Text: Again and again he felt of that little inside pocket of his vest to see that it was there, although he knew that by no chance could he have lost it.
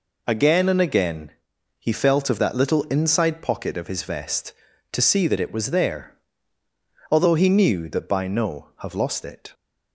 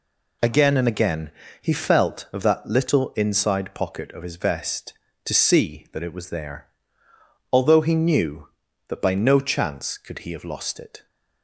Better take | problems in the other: second | pauses between "again" and "he"; noticeable; at 1.3 s; 0.50 s long; slight in the second // skips "chance could he"; at 8.7 s

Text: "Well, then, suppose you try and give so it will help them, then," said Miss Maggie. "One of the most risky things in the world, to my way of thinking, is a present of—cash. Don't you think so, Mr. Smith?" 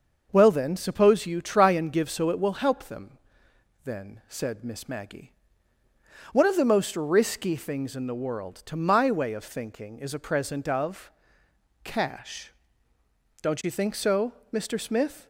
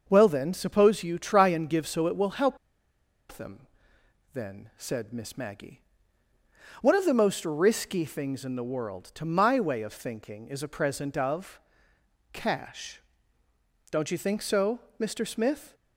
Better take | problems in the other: first | starts louder than the rest; noticeable; until 1.0 s; 6 dB; noticeable in the first // pauses between "help" and "them"; noticeable; at 2.5 s; 0.74 s long

